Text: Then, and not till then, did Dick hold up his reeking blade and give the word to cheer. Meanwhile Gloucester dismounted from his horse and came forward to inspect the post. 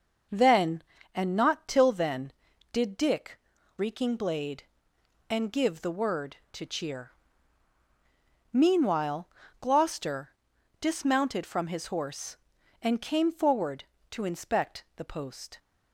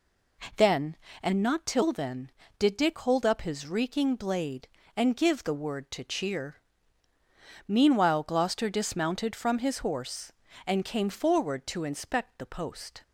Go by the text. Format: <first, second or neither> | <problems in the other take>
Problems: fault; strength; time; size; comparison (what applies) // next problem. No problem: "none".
second | skips "hold up his"; at 3.5 s // pauses between "Meanwhile" and "Gloucester"; slight; at 9.2 s; 0.32 s long // pauses between "Gloucester" and "dismounted"; noticeable; at 10.3 s; 0.50 s long